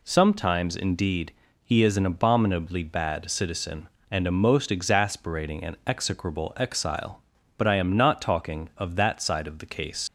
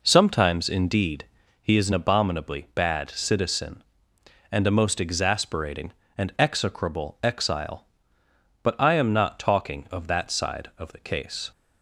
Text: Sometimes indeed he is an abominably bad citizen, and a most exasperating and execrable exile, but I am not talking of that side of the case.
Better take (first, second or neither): second